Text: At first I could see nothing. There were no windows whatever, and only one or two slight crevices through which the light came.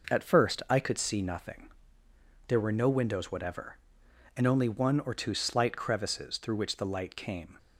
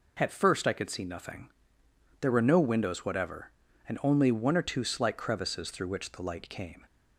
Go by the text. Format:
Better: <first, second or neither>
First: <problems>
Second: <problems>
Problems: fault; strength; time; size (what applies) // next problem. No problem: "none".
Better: neither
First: none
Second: none